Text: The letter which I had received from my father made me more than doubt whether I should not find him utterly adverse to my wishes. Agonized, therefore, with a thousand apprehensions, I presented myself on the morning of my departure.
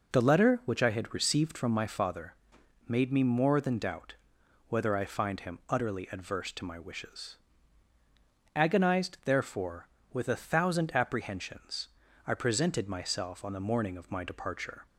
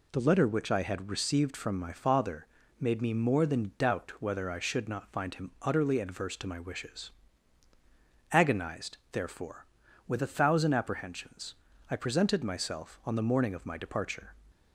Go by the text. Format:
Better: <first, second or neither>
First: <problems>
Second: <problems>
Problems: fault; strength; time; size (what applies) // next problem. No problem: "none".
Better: second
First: pauses between "father" and "made"; noticeable; at 2.3 s; 0.50 s long // pauses between "doubt" and "whether"; noticeable; at 4.1 s; 0.52 s long // skips "should not"; at 5.0 s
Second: pauses between "father" and "made"; slight; at 2.4 s; 0.32 s long